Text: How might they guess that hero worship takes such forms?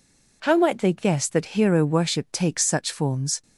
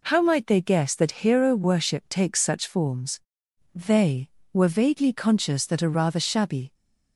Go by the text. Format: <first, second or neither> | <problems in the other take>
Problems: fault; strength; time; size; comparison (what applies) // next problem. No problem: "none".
first | goes on to say "They were vaguely conscious that a rather shabby"; strong; from 3.7 s on; 3.0 s long